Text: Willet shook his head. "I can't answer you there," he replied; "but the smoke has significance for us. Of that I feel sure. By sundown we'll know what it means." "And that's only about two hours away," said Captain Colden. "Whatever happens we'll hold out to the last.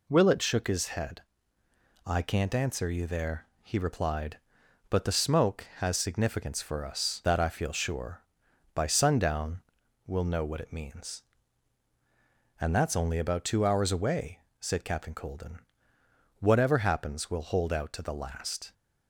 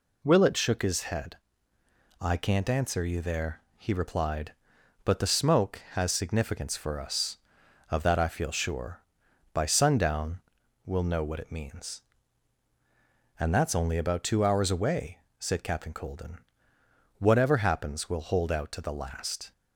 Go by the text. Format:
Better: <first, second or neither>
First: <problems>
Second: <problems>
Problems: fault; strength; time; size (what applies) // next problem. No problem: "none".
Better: second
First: skips "Of"; at 7.2 s // pauses between "sundown" and "we'll"; at 9.6 s; 0.42 s long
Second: pauses between "sundown" and "we'll"; at 10.4 s; 0.42 s long